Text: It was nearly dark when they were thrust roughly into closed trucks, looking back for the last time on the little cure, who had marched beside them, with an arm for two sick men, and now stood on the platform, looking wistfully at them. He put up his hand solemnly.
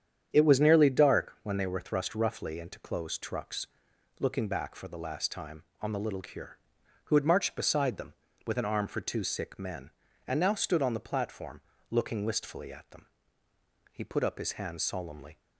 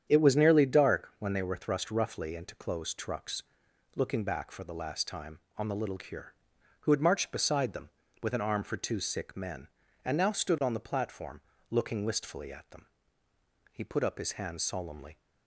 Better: neither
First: starts louder than the rest; strong; until 1.3 s; 8.5 dB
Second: starts louder than the rest; strong; until 1.1 s; 8.5 dB

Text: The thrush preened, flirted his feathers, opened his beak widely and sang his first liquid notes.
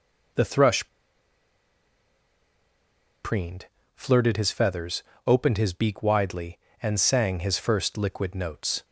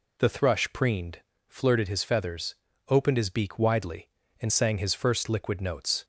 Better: second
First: pauses between "thrush" and "preened"; strong; at 0.8 s; 2.3 s long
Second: none

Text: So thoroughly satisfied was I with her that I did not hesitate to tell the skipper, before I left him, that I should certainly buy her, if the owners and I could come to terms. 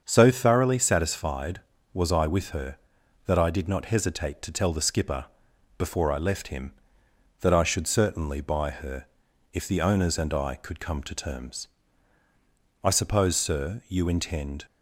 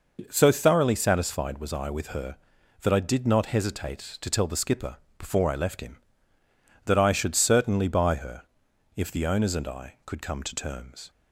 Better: second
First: starts louder than the rest; until 1.0 s; 7 dB // goes on to say "I suppose sir you intend"; strong; from 12.8 s on; 1.8 s long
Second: none

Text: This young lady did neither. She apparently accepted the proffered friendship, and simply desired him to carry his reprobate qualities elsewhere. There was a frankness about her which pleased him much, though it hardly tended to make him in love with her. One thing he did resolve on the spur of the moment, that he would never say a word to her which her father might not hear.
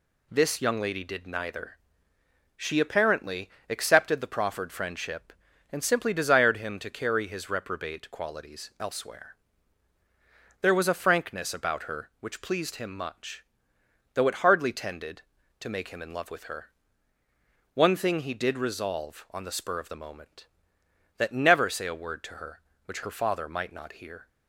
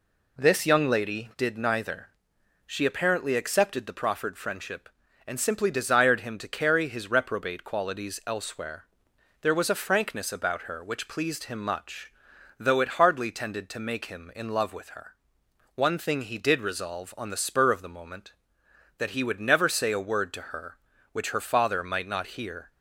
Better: second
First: pauses between "apparently" and "accepted"; slight; at 3.4 s; 0.22 s long // skips "he would"; at 21.3 s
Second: none

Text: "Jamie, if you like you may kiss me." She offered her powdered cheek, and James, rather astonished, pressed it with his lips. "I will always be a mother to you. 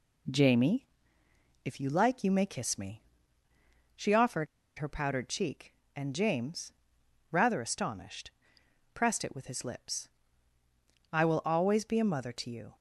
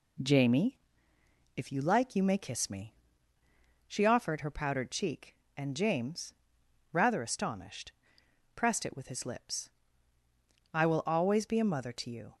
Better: second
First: pauses between "offered" and "her"; slight; at 4.4 s; 0.32 s long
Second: none

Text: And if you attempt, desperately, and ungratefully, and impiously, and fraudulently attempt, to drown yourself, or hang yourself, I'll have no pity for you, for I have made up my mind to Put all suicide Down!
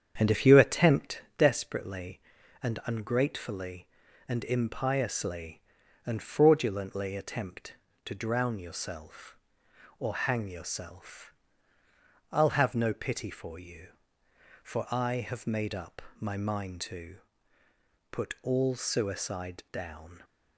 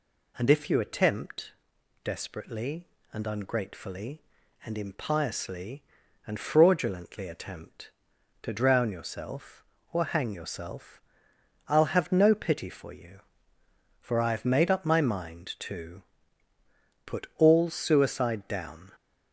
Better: second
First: starts louder than the rest; strong; until 1.4 s; 8 dB // pauses between "up" and "my"; slight; at 16.0 s; 0.18 s long // pauses between "to" and "Put"; noticeable; at 17.1 s; 0.94 s long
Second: pauses between "to" and "Put"; at 16.0 s; 1.0 s long

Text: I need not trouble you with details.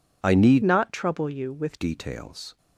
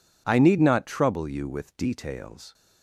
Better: second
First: changes voice from "not" to "with"; from 0.6 to 1.7 s; 1.1 s long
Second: none

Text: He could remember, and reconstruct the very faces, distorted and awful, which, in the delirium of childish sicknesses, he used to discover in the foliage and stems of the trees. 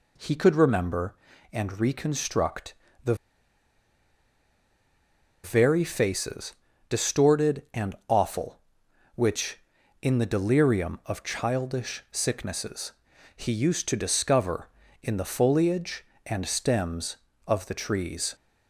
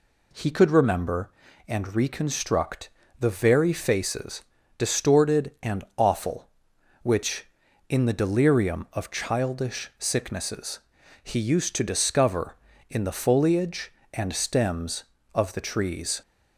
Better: second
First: pauses between "reconstruct" and "the"; slight; at 2.7 s; 0.32 s long // pauses between "the" and "very"; strong; at 3.1 s; 2.2 s long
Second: pauses between "reconstruct" and "the"; slight; at 2.8 s; 0.32 s long

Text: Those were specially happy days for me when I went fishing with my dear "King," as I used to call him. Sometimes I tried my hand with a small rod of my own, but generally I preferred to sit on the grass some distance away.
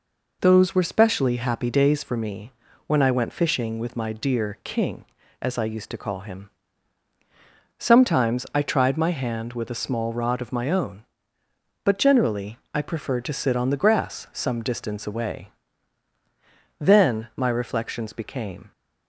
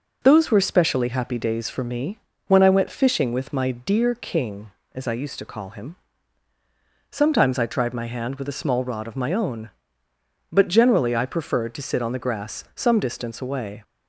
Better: second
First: pauses between "me" and "when"; slight; at 2.5 s; 0.36 s long // pauses between "generally" and "I"; slight; at 12.5 s; 0.16 s long // goes on to say "Then my reflections became"; strong; from 16.7 s on; 1.9 s long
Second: pauses between "me" and "when"; slight; at 2.1 s; 0.28 s long

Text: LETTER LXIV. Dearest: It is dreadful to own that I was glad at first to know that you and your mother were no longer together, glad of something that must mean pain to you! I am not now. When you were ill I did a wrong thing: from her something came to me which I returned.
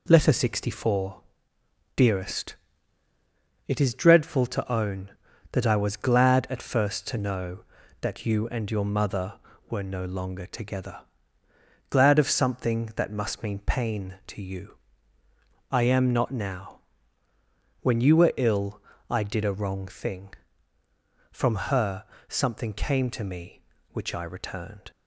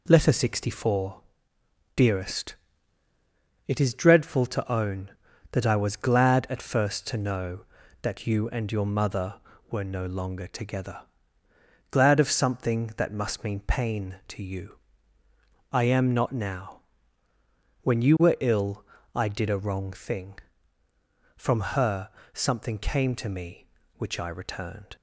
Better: neither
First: pauses between "ill" and "I"; slight; at 18.7 s; 0.28 s long // pauses between "from" and "her"; slight; at 21.5 s; 0.16 s long // pauses between "her" and "something"; slight; at 22.0 s; 0.24 s long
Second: pauses between "ill" and "I"; slight; at 18.8 s; 0.30 s long // pauses between "from" and "her"; slight; at 21.5 s; 0.16 s long // pauses between "her" and "something"; slight; at 22.0 s; 0.24 s long

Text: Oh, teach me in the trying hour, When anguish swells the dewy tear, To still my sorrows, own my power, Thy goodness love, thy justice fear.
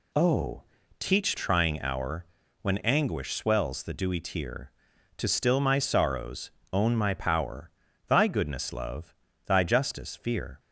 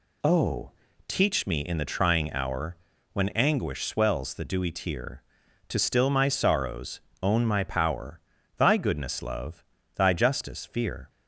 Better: second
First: skips "me in the"; at 1.3 s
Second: none

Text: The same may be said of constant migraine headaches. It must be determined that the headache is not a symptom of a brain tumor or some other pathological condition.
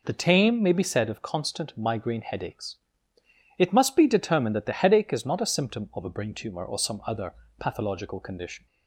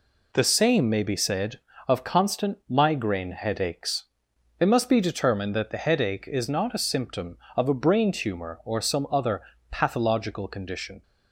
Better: second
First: says "tame" for "same"; at 0.1 s // pauses between "other" and "pathological"; slight; at 7.3 s; 0.26 s long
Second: pauses between "other" and "pathological"; slight; at 9.4 s; 0.30 s long

